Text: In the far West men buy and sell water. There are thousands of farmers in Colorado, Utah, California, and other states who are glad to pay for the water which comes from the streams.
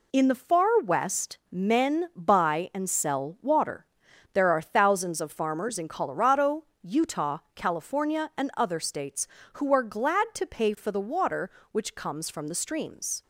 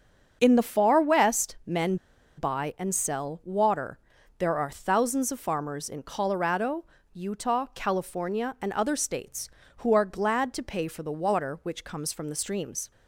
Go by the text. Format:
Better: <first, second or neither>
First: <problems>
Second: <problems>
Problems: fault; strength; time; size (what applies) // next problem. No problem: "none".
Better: first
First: none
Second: starts louder than the rest; until 1.4 s; 6.5 dB // pauses between "men" and "buy"; at 1.9 s; 0.42 s long